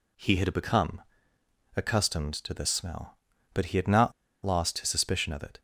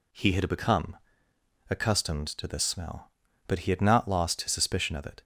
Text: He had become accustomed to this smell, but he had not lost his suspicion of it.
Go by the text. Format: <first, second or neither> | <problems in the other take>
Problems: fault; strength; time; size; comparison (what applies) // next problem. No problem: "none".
second | pauses between "become" and "accustomed"; noticeable; at 1.0 s; 0.74 s long; noticeable in the second // pauses between "not" and "lost"; slight; at 4.1 s; 0.33 s long